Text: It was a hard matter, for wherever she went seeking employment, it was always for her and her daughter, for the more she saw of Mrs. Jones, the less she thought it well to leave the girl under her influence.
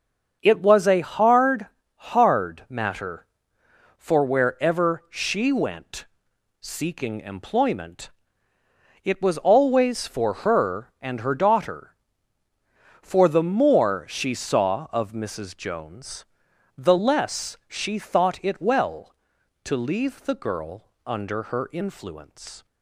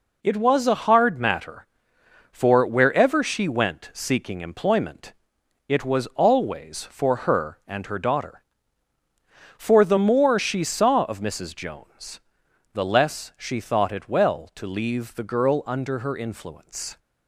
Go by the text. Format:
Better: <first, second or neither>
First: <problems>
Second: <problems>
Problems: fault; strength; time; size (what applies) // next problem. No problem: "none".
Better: second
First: starts louder than the rest; until 1.4 s; 6.5 dB // says "hard" twice; at 2.1 s // pauses between "went" and "seeking"; noticeable; at 6.0 s; 0.56 s long // pauses between "girl" and "under"; slight; at 20.8 s; 0.18 s long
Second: none